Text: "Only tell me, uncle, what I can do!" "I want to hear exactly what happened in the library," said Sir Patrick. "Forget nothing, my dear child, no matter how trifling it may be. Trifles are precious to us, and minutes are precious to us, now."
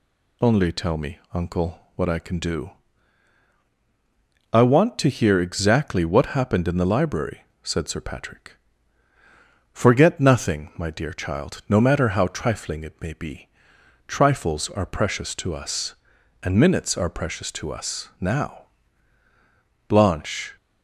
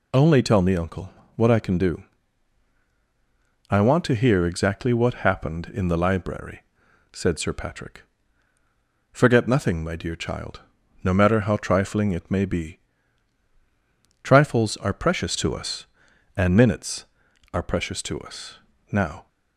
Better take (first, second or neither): second